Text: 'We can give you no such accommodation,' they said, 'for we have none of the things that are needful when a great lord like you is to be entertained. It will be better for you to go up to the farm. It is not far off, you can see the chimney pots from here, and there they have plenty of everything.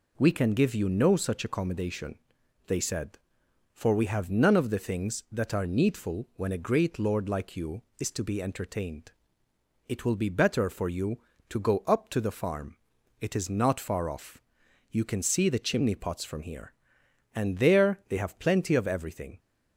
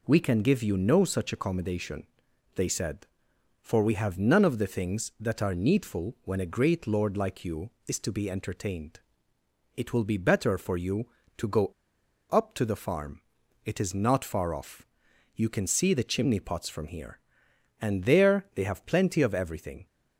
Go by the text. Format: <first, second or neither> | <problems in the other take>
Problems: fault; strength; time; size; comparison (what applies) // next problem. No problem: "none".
first | pauses between "go" and "up"; noticeable; at 11.7 s; 0.58 s long